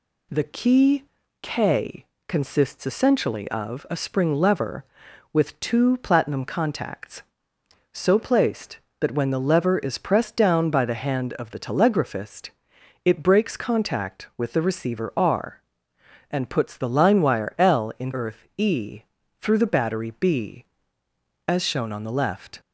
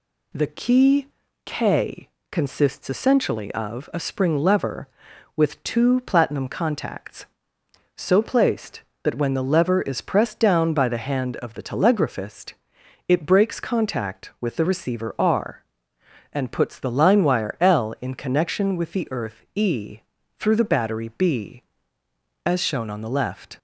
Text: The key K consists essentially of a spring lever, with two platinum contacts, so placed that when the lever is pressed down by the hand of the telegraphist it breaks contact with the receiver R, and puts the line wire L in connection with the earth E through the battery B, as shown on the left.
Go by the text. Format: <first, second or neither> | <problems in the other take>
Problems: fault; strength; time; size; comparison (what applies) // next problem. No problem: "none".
second | pauses between "key" and "K"; slight; at 1.0 s; 0.36 s long; slight in the second // pauses between "K" and "consists"; slight; at 2.0 s; 0.22 s long; slight in the second // pauses between "telegraphist" and "it"; noticeable; at 12.4 s; 0.54 s long; noticeable in the second // skips "connection with the"; at 18.1 s // pauses between "E" and "through"; at 19.0 s; 0.38 s long; also in the second